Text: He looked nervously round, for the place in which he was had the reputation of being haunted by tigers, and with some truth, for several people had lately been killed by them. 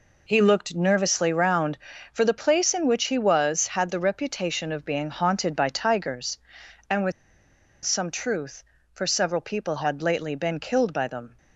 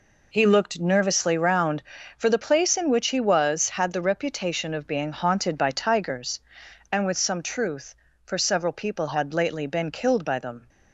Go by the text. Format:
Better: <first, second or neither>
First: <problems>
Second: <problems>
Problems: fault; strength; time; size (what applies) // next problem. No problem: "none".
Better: second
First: pauses between "with" and "some"; noticeable; at 7.1 s; 0.72 s long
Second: none